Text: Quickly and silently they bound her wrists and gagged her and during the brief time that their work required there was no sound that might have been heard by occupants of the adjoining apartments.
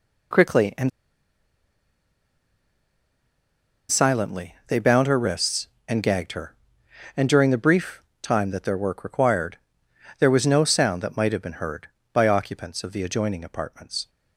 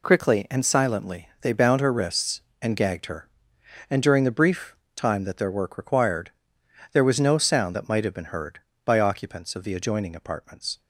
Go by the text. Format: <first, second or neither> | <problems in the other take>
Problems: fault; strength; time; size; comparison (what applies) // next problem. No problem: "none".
second | pauses between "and" and "silently"; strong; at 0.8 s; 2.9 s long // pauses between "brief" and "time"; slight; at 8.0 s; 0.18 s long; slight in the second // pauses between "required" and "there"; noticeable; at 9.5 s; 0.62 s long; noticeable in the second